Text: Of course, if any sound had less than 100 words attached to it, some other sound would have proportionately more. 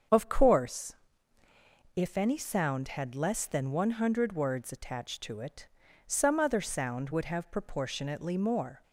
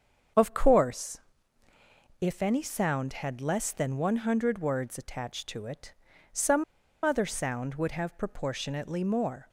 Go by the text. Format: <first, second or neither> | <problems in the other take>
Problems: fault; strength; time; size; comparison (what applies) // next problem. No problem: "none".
first | starts louder than the rest; strong; until 2.3 s; 7 dB; also in the first // pauses between "some" and "other"; at 6.6 s; 0.40 s long